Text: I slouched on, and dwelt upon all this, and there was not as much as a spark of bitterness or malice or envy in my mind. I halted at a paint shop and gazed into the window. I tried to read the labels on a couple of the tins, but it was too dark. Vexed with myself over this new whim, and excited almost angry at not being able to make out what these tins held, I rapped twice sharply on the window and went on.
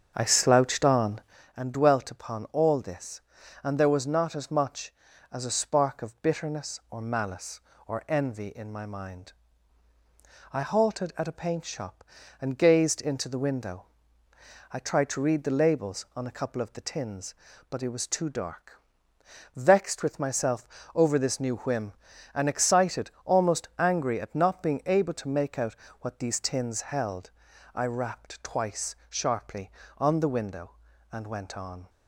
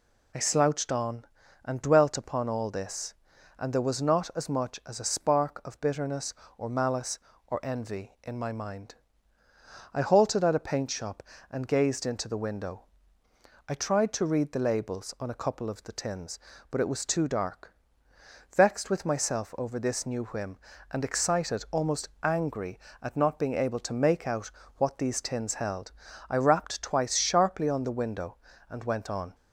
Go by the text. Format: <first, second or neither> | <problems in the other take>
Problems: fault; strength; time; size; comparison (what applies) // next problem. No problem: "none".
second | starts louder than the rest; until 1.5 s; 7 dB // pauses between "myself" and "over"; slight; at 20.6 s; 0.28 s long // pauses between "out" and "what"; slight; at 25.7 s; 0.26 s long; slight in the second